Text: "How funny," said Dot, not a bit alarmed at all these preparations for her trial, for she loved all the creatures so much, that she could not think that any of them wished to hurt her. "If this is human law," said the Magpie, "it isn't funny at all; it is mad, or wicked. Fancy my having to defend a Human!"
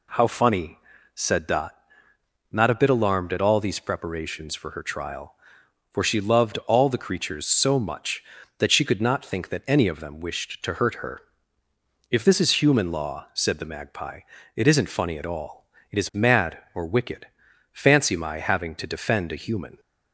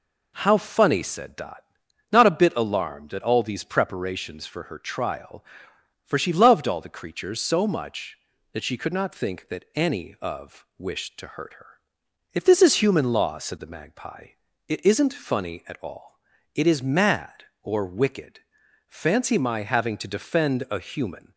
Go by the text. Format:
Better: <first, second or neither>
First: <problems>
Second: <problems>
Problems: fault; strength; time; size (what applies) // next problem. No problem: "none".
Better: first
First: none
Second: skips "them"; at 10.7 s